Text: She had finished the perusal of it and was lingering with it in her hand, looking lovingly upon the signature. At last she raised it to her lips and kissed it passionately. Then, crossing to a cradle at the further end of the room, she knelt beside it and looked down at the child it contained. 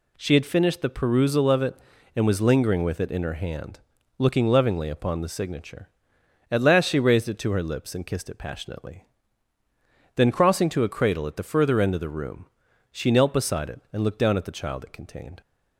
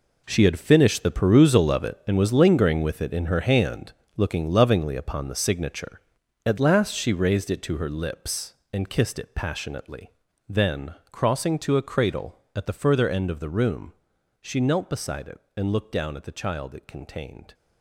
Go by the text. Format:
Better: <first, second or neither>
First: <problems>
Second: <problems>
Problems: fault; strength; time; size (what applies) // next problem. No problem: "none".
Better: first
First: none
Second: gets quieter; strong; throughout; 12 dB